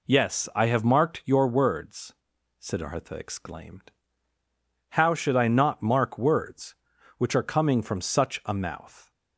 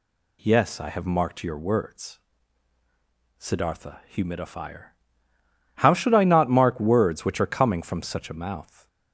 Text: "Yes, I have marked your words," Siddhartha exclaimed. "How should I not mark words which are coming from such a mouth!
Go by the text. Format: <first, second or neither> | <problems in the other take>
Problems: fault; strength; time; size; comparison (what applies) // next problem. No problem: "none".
first | says "humidifier" for "exclaimed"; at 4.1 s